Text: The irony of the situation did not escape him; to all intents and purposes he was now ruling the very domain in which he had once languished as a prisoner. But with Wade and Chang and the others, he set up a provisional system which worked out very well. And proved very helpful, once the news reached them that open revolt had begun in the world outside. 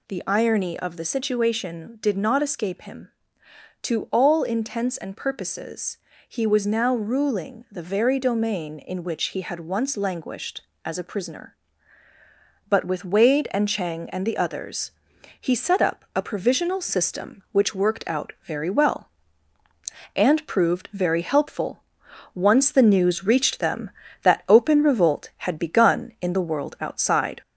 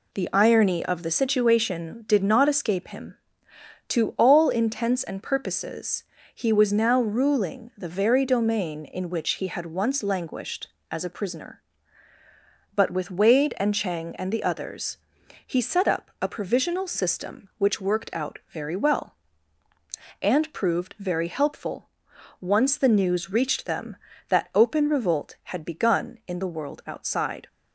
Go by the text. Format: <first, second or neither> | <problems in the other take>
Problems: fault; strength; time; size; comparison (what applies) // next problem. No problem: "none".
second | gets louder; slight; throughout; 2 dB // pauses between "purposes" and "he"; slight; at 5.9 s; 0.32 s long; slight in the second